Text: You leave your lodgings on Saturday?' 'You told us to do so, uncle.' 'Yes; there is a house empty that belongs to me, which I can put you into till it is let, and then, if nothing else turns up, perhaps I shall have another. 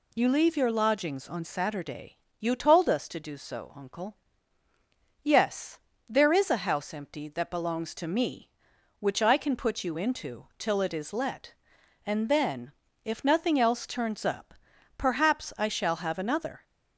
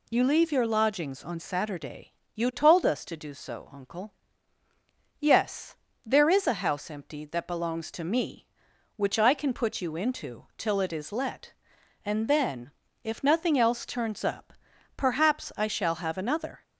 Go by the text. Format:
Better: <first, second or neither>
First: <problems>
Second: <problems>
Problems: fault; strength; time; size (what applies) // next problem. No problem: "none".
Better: neither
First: none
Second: none